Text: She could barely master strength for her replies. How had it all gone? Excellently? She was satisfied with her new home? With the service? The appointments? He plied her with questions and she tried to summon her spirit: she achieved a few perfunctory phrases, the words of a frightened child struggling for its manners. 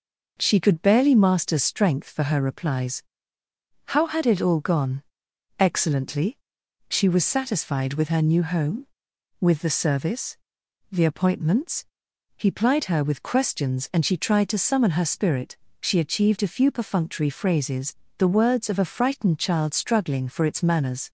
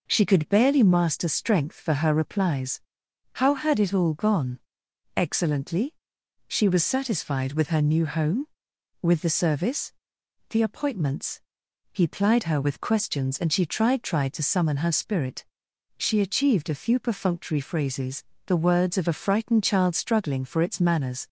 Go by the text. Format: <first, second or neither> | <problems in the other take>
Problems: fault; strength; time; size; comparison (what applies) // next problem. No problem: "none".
first | says "tried" twice; at 14.0 s